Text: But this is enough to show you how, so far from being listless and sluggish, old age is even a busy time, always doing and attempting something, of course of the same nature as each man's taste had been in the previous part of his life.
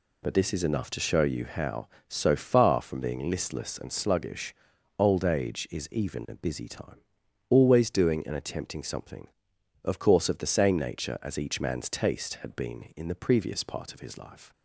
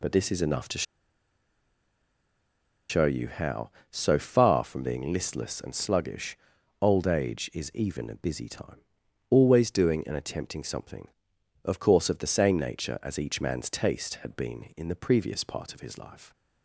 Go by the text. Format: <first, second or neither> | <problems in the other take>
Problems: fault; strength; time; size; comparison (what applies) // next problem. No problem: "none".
first | pauses between "to" and "show"; strong; at 0.8 s; 2.0 s long